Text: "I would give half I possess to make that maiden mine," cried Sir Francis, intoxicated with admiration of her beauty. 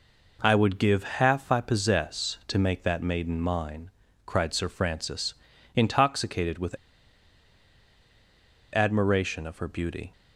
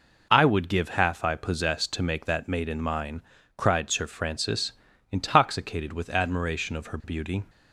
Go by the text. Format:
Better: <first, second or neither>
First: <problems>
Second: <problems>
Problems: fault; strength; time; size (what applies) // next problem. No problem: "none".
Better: second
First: pauses between "with" and "admiration"; strong; at 6.7 s; 1.9 s long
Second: none